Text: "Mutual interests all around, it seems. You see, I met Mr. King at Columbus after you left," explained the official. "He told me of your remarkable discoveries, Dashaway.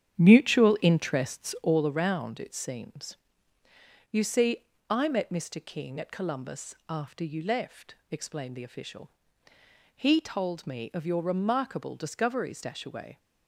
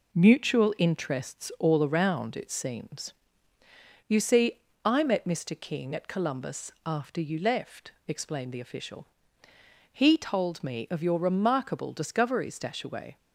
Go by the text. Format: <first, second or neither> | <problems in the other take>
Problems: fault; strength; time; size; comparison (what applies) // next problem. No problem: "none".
second | starts louder than the rest; strong; until 1.8 s; 9 dB // pauses between "Columbus" and "after"; slight; at 6.7 s; 0.16 s long; slight in the second